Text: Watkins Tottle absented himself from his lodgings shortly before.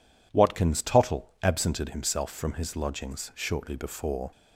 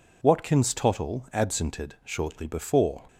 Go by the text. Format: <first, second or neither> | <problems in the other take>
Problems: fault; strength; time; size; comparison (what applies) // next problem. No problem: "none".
first | skips "himself from his lodgings"; at 1.9 s